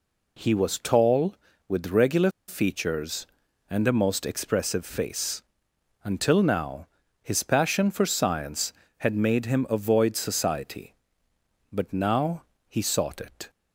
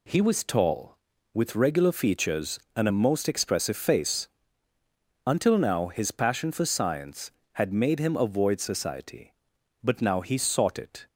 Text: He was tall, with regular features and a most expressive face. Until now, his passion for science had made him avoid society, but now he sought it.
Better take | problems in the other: second | pauses between "regular" and "features"; slight; at 2.2 s; 0.18 s long // pauses between "now" and "he"; slight; at 12.4 s; 0.24 s long

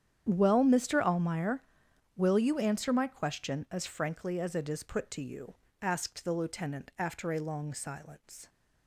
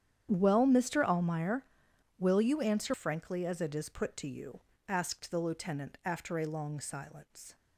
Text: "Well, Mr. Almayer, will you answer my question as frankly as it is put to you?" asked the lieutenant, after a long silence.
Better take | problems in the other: first | starts louder than the rest; strong; until 1.3 s; 9.5 dB; strong in the first // skips "my question as"; at 2.9 s

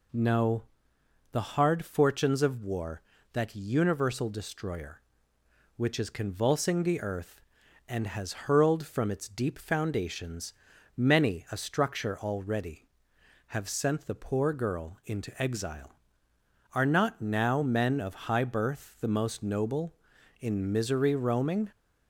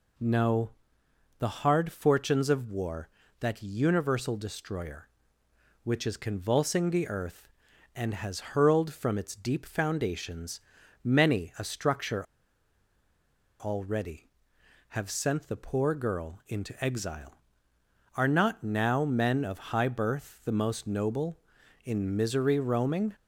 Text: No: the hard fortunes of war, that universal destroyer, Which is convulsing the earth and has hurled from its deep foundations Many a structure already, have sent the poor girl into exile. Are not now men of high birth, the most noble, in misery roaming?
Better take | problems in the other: first | pauses between "foundations" and "Many"; noticeable; at 10.5 s; 0.46 s long; noticeable in the first // pauses between "structure" and "already"; strong; at 12.2 s; 1.3 s long

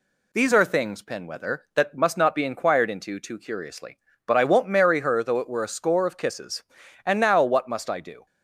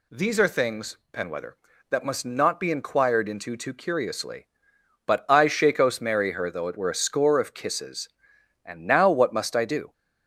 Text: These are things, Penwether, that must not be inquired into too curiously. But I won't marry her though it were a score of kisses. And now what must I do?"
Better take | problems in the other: first | says "shakos" for "won't"; at 5.4 s

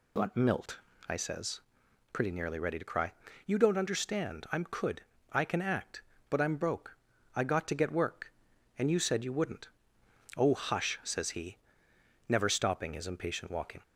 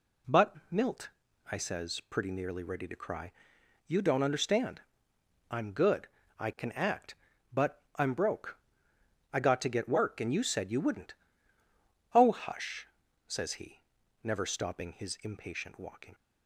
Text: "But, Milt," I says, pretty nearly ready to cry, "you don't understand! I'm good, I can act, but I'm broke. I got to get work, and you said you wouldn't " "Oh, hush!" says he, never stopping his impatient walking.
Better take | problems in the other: second | says "could" for "good"; at 4.6 s

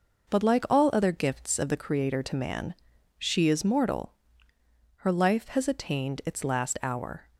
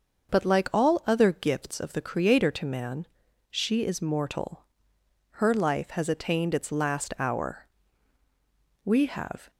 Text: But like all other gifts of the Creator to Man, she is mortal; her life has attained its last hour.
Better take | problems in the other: first | starts louder than the rest; until 1.3 s; 6.5 dB // goes on to say "We have"; noticeable; from 8.8 s on; 0.66 s long

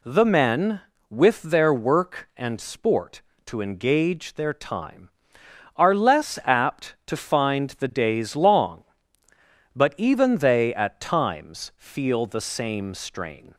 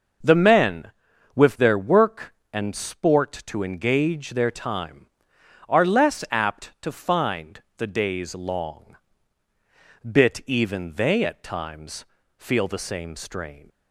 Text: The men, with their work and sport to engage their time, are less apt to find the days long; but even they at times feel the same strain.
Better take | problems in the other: first | pauses between "find" and "the"; slight; at 7.6 s; 0.16 s long // says "bit" for "but"; at 10.0 s // pauses between "times" and "feel"; slight; at 12.0 s; 0.32 s long

